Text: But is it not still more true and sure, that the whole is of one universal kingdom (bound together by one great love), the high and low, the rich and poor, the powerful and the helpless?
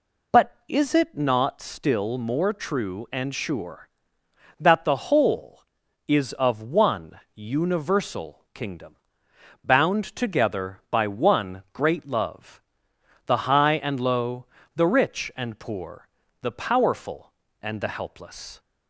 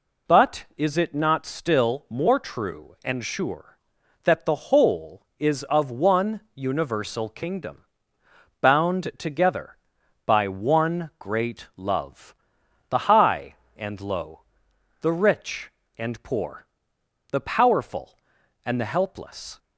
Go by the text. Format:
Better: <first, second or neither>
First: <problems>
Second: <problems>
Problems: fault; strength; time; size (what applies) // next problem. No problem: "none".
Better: neither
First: none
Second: none